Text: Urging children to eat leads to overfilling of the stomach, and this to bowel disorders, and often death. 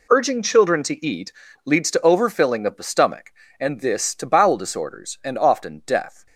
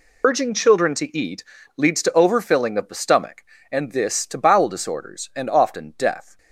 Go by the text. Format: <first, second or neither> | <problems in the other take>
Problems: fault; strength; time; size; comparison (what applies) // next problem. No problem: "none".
first | loses the start of "Urging"; at 0.2 s; 30 ms // pauses between "eat" and "leads"; slight; at 1.4 s; 0.32 s long; slight in the first